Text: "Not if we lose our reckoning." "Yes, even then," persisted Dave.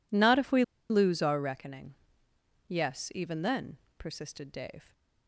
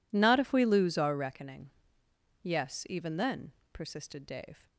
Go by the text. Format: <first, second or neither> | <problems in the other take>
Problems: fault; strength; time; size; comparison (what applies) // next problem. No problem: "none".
second | pauses between "we" and "lose"; slight; at 0.6 s; 0.26 s long